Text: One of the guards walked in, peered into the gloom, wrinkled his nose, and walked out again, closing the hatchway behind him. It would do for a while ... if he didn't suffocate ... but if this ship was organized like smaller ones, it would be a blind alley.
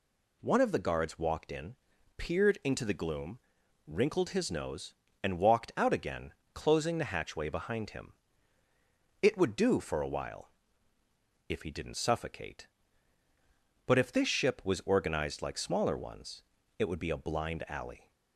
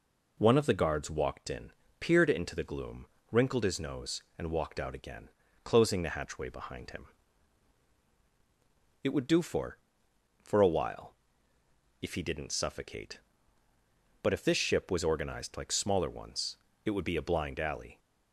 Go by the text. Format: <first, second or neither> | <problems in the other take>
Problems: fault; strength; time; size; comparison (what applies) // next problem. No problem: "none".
first | says "for" twice; at 10.4 s